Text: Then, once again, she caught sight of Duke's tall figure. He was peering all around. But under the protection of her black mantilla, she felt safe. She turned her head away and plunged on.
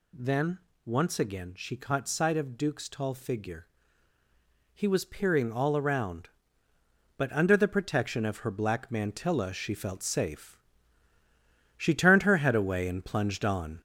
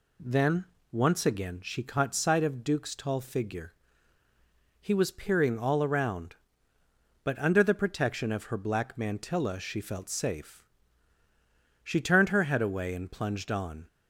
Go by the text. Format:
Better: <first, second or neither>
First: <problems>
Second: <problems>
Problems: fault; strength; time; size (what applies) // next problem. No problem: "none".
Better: second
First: gets louder; noticeable; throughout; 4.5 dB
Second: none